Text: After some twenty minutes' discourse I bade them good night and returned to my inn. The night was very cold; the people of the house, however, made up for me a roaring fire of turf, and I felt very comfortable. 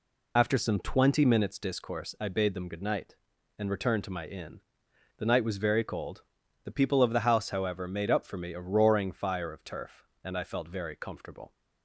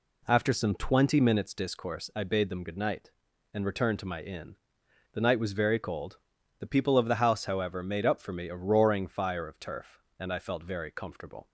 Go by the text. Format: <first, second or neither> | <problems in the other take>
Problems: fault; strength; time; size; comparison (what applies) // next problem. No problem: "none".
second | loses the start of "After"; at 0.3 s; 70 ms